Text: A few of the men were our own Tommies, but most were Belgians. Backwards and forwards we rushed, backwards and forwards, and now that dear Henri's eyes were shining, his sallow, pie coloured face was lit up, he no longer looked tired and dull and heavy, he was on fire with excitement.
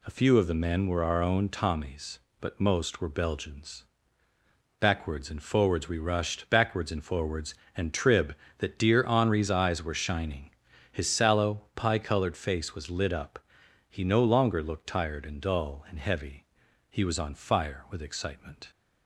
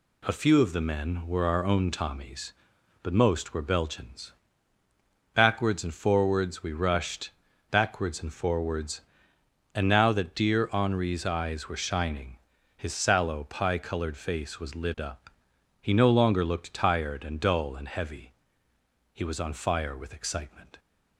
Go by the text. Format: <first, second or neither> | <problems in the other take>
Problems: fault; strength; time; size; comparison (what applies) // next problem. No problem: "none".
second | says "trib" for "now"; at 7.9 s